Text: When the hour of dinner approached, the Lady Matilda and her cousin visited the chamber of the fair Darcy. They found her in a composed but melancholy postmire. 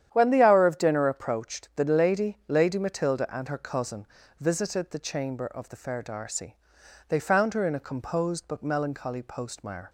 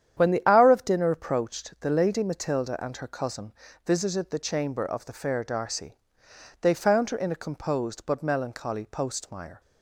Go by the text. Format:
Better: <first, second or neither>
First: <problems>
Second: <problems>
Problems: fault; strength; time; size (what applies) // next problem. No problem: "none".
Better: second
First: starts louder than the rest; strong; until 1.1 s; 10 dB // says "Lady" twice; at 2.4 s // pauses between "cousin" and "visited"; slight; at 4.0 s; 0.34 s long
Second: starts louder than the rest; strong; until 1.2 s; 9.5 dB // pauses between "cousin" and "visited"; slight; at 3.5 s; 0.34 s long